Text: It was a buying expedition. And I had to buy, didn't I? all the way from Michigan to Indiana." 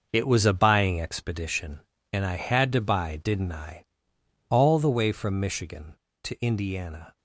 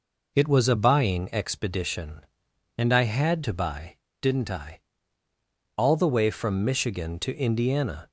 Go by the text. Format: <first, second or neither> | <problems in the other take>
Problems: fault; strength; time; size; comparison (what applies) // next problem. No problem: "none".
second | gets quieter; strong; throughout; 11.5 dB